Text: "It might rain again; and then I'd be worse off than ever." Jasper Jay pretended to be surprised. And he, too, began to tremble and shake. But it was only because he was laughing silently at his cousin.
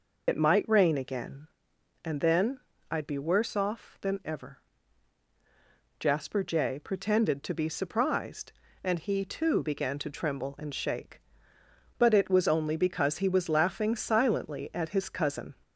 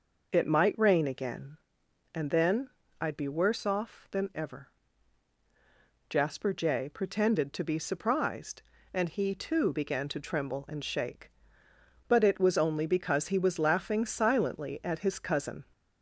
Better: second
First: loses the start of "It"; at 0.2 s; 60 ms // pauses between "then" and "I'd"; slight; at 2.5 s; 0.30 s long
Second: pauses between "then" and "I'd"; slight; at 2.6 s; 0.30 s long

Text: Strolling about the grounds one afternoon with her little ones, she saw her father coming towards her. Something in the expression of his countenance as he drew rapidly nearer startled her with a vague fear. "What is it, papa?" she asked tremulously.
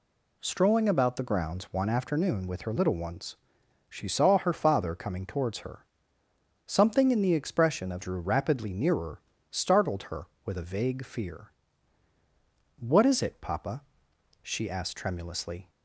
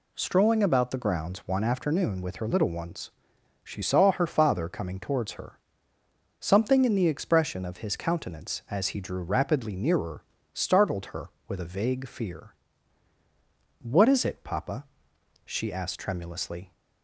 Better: second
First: skips "his countenance as he"; at 8.0 s // pauses between "nearer" and "startled"; slight; at 9.1 s; 0.30 s long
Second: pauses between "nearer" and "startled"; slight; at 10.2 s; 0.30 s long

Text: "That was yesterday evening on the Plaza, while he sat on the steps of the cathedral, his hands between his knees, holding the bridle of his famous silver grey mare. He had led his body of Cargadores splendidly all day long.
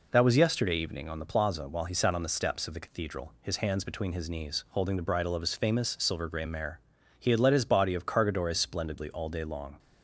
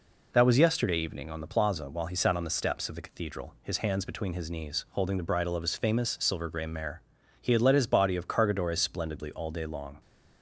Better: neither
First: none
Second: none

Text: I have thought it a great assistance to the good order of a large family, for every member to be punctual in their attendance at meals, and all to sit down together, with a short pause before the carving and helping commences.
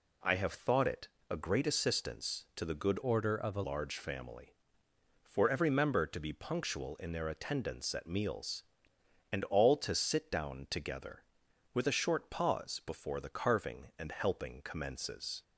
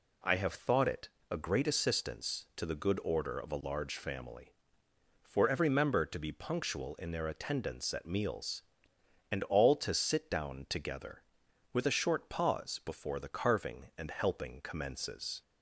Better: second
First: pauses between "it" and "a"; slight; at 1.0 s; 0.24 s long // changes voice from "order" to "a"; from 3.0 to 3.6 s; 0.6 s long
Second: pauses between "it" and "a"; slight; at 1.0 s; 0.24 s long

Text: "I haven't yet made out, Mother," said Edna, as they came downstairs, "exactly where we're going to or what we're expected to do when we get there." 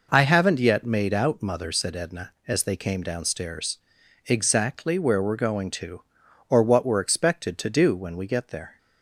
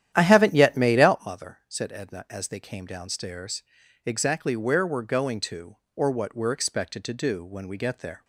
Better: first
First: none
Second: starts louder than the rest; strong; until 1.4 s; 11 dB

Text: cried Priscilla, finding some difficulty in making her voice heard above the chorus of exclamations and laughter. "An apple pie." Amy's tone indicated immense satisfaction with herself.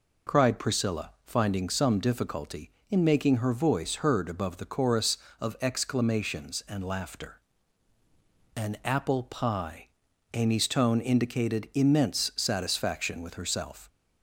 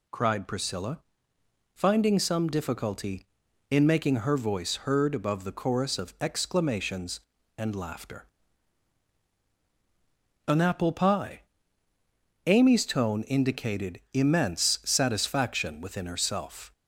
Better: first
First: none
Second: says "within" for "with"; at 15.8 s

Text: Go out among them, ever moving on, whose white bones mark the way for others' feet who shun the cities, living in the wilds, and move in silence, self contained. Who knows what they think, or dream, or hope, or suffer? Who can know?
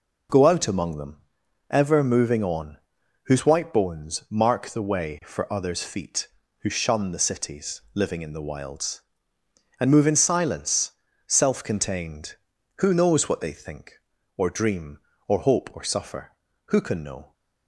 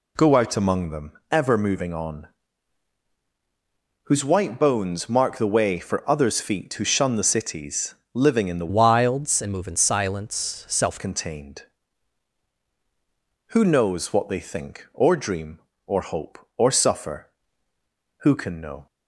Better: first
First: none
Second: changes voice from "wilds" to "self"; from 8.6 to 11.0 s; 2.4 s long

